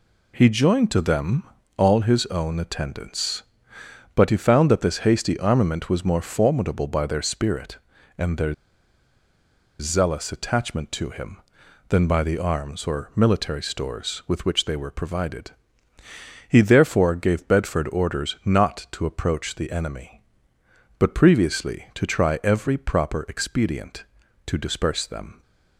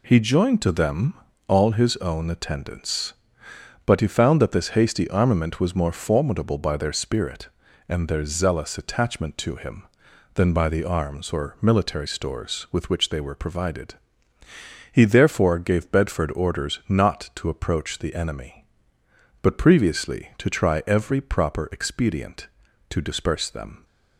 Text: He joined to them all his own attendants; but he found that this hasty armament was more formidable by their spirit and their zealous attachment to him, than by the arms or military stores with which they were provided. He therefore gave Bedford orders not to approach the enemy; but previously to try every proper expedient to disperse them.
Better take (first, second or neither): second